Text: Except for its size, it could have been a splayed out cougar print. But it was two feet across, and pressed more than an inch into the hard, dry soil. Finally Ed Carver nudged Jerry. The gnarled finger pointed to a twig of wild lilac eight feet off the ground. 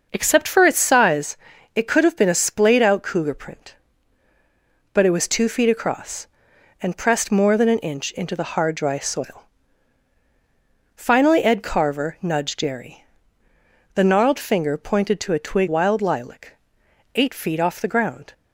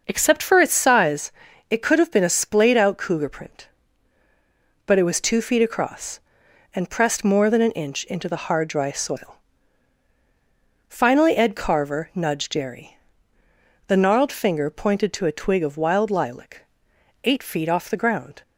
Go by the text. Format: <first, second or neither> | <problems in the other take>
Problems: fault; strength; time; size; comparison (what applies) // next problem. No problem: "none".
second | starts louder than the rest; noticeable; until 1.1 s; 6 dB // skips "of"; at 15.6 s // pauses between "lilac" and "eight"; noticeable; at 16.5 s; 0.60 s long; noticeable in the second